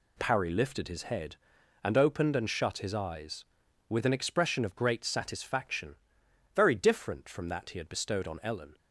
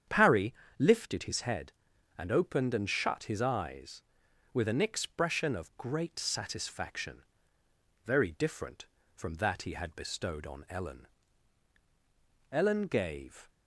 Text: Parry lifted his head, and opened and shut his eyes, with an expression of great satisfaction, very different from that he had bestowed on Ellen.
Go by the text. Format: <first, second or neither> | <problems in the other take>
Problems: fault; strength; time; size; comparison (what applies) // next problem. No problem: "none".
first | starts louder than the rest; strong; until 1.3 s; 8.5 dB // pauses between "Parry" and "lifted"; slight; at 0.5 s; 0.26 s long // goes on to say "Ellen gave"; noticeable; from 12.5 s on; 0.98 s long